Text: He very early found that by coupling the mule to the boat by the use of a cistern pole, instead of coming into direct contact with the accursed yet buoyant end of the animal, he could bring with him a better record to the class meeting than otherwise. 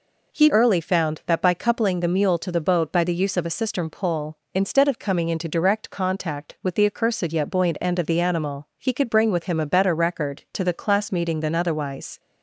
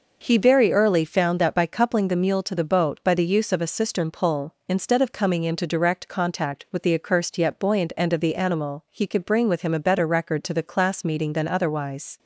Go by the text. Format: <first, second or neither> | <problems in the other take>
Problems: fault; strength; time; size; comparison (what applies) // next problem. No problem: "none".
second | skips "very"; at 0.4 s